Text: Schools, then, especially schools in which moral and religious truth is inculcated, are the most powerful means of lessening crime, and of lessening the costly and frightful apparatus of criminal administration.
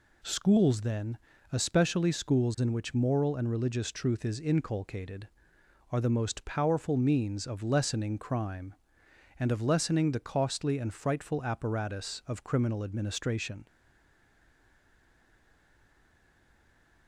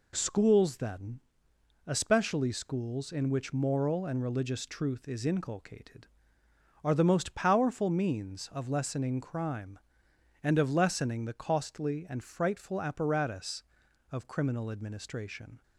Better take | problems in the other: second | stays silent after the last word; strong; from 13.6 s on; 3.4 s long

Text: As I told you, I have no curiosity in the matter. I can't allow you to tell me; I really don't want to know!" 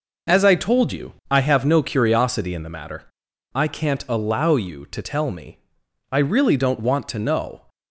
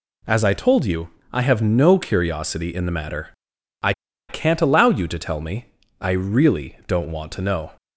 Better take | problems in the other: first | pauses between "I" and "can't"; at 3.9 s; 0.37 s long

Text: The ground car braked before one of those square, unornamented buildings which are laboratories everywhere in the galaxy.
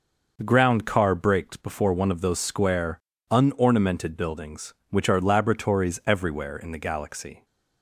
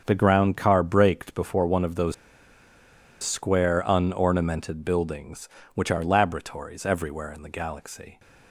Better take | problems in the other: first | starts louder than the rest; until 1.0 s; 7 dB // pauses between "those" and "square"; at 2.1 s; 1.0 s long

